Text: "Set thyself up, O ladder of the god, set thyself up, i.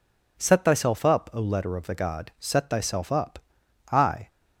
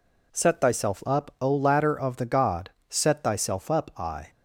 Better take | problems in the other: second | says "letter" for "ladder"; at 1.4 s

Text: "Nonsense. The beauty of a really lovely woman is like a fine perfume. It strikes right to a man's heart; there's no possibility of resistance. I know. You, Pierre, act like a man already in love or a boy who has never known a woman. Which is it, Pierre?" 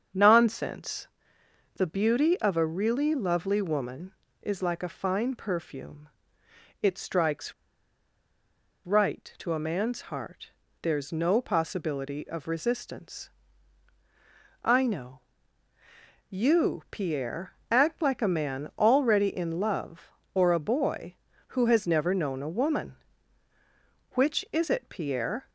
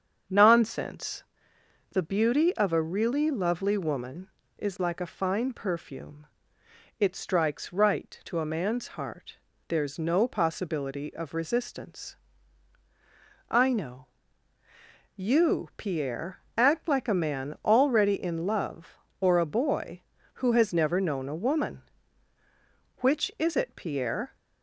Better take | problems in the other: second | starts louder than the rest; strong; until 1.8 s; 7.5 dB; strong in the second // pauses between "strikes" and "right"; strong; at 7.5 s; 1.3 s long

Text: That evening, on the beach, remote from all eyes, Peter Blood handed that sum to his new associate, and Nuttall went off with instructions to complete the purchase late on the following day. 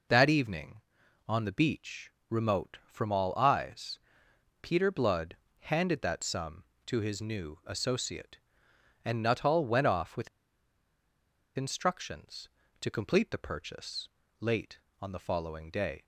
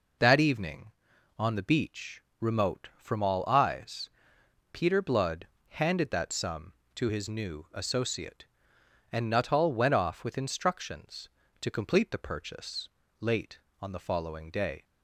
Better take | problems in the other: second | pauses between "Blood" and "handed"; slight; at 5.3 s; 0.24 s long; slight in the second // pauses between "with" and "instructions"; strong; at 10.2 s; 1.2 s long // pauses between "purchase" and "late"; slight; at 14.0 s; 0.32 s long; slight in the second

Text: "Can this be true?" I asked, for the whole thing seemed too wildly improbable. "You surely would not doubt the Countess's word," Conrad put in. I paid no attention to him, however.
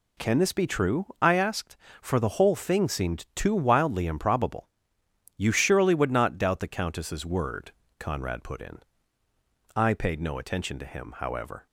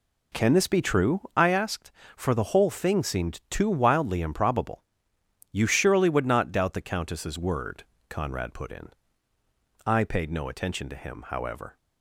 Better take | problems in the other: first | starts louder than the rest; until 1.4 s; 3.5 dB

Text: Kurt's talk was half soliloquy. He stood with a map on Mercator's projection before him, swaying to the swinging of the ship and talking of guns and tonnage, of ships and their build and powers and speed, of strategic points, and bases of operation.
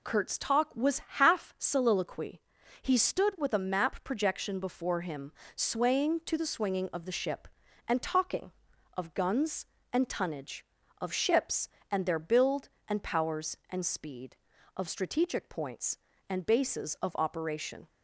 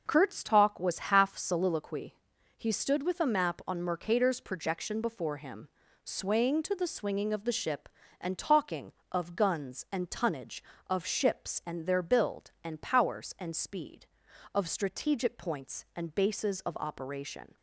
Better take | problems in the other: second | skips "on Mercator's"; at 4.0 s

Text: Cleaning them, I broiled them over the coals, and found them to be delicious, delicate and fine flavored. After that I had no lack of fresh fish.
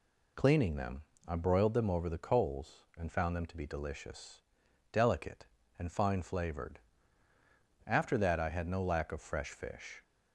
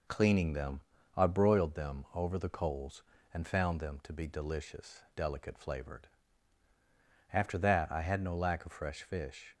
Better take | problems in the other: first | skips "and fine"; at 5.5 s

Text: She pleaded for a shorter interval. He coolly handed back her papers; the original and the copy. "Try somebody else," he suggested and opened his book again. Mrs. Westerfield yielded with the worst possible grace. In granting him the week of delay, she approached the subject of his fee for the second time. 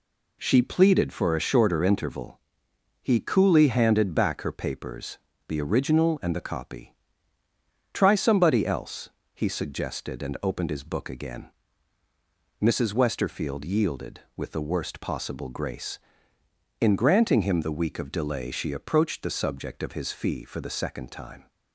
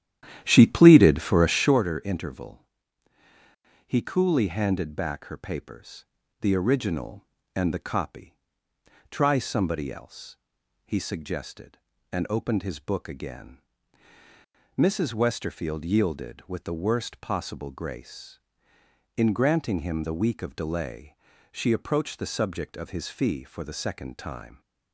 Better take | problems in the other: first | starts louder than the rest; strong; until 1.8 s; 11.5 dB

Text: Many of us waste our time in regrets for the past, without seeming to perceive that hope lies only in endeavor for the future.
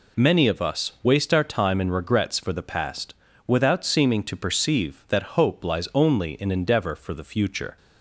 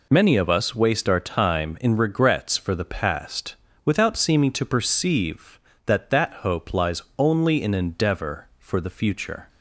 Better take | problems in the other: first | says "that" twice; at 6.0 s // pauses between "lies" and "only"; slight; at 7.0 s; 0.16 s long

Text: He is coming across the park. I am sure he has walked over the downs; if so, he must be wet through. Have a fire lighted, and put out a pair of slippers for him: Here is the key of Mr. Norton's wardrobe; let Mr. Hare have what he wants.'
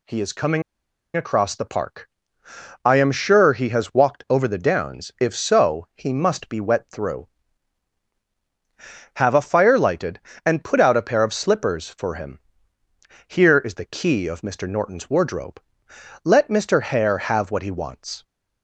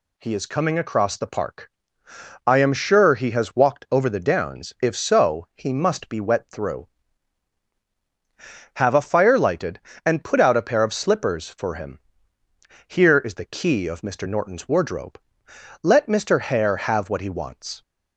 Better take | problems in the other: second | pauses between "coming" and "across"; noticeable; at 0.6 s; 0.54 s long

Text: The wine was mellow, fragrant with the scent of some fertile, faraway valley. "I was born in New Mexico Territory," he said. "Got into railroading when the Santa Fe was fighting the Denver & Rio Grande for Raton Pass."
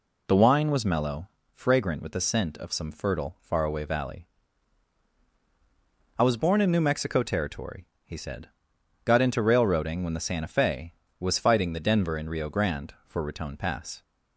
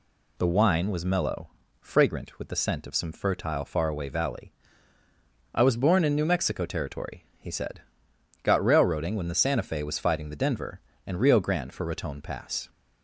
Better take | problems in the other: first | skips "into"; at 8.6 s

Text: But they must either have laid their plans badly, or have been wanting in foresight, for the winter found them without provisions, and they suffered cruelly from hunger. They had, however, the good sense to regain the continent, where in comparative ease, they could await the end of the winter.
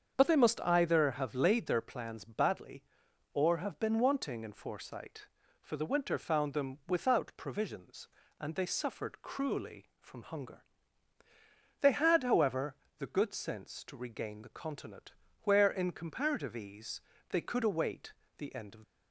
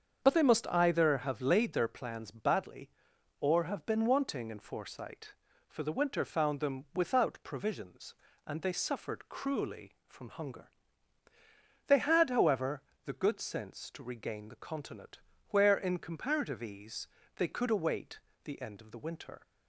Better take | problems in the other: second | starts louder than the rest; strong; until 1.1 s; 7 dB; strong in the second // pauses between "await" and "the"; slight; at 18.1 s; 0.24 s long; slight in the second // stops before "the winter"; at 18.8 s

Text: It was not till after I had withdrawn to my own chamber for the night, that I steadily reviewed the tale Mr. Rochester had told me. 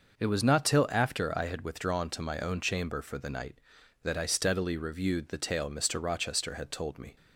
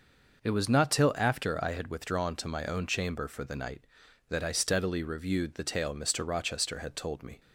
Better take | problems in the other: neither | none

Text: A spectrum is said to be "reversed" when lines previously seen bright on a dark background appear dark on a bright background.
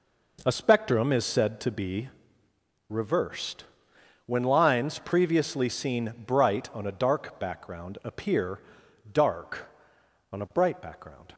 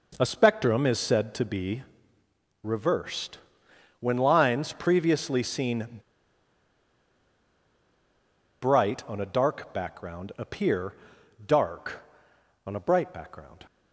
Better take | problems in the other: first | pauses between "be" and "reversed"; noticeable; at 1.8 s; 0.80 s long; noticeable in the first // pauses between "reversed" and "when"; noticeable; at 3.3 s; 0.60 s long; noticeable in the first // pauses between "seen" and "bright"; strong; at 5.8 s; 2.7 s long // pauses between "appear" and "dark"; noticeable; at 10.9 s; 0.50 s long; noticeable in the first

